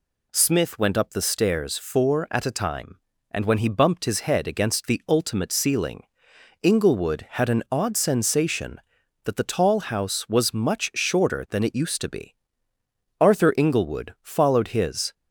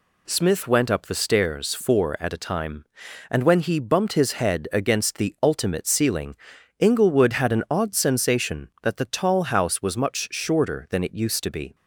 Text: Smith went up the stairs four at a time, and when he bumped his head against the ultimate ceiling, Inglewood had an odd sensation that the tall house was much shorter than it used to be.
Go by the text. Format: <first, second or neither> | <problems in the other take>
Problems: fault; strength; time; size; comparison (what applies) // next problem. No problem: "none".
second | goes on to say "Arthur Inglewood followed his"; strong; from 13.1 s on; 1.9 s long